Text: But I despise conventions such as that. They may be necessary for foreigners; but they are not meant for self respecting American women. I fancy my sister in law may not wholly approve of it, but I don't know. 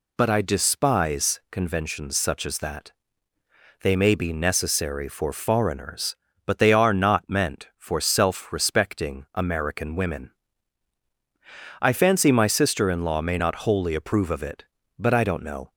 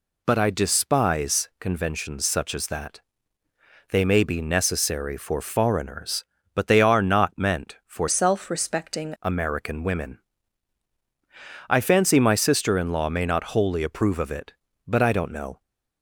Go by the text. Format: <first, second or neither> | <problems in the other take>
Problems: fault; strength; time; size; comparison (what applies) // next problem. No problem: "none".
first | changes voice from "self" to "respecting"; from 8.0 to 9.1 s; 1.1 s long